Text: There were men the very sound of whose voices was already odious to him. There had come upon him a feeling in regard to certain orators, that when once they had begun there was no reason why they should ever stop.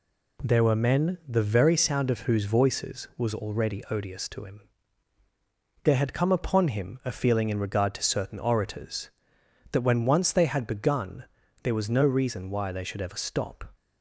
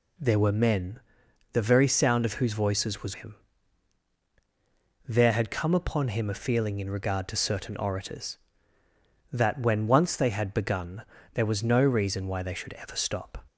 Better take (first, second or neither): first